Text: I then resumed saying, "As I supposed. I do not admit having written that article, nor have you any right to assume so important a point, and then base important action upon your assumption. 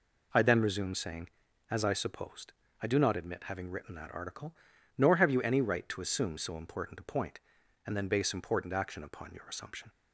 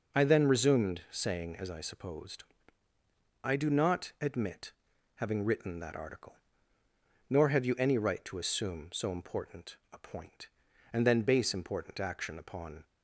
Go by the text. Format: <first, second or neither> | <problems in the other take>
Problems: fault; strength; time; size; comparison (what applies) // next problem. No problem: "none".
first | pauses between "admit" and "having"; at 4.7 s; 0.42 s long // pauses between "important" and "a"; slight; at 9.7 s; 0.16 s long // stops before "your assumption"; at 12.8 s